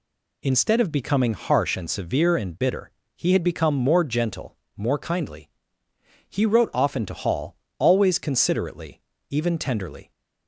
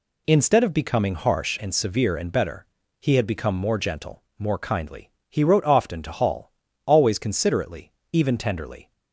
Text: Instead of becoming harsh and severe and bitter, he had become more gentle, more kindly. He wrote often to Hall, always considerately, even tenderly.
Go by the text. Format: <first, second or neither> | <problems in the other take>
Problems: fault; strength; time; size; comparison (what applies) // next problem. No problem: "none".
first | says "better" for "bitter"; at 2.3 s